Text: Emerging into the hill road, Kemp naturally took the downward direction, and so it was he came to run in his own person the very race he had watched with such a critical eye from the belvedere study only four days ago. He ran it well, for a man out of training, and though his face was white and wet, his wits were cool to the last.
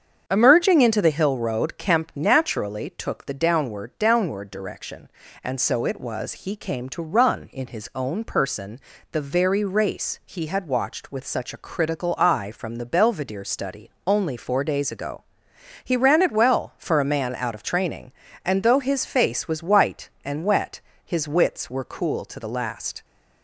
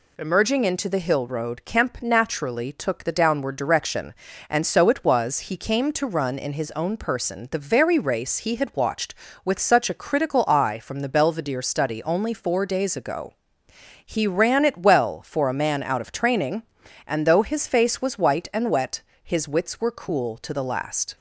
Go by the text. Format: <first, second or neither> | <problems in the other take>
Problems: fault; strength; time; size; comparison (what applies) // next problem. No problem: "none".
second | starts louder than the rest; strong; until 1.2 s; 7.5 dB // says "downward" twice; at 4.0 s // pauses between "person" and "the"; slight; at 8.8 s; 0.32 s long // pauses between "study" and "only"; slight; at 13.8 s; 0.16 s long